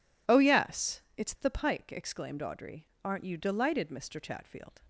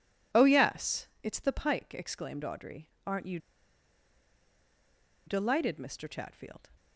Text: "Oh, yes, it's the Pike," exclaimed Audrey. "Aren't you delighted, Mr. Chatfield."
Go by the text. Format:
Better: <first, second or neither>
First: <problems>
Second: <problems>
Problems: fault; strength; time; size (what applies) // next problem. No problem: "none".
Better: first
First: none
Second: pauses between "you" and "delighted"; strong; at 3.3 s; 1.8 s long